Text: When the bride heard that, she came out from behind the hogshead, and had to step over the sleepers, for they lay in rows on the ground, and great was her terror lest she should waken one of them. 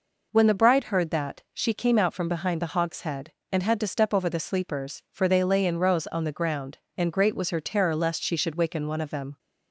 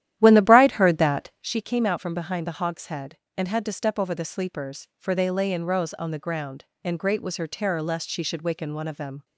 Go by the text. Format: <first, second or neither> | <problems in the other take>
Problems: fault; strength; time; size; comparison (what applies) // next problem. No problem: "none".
first | starts louder than the rest; strong; until 1.5 s; 12 dB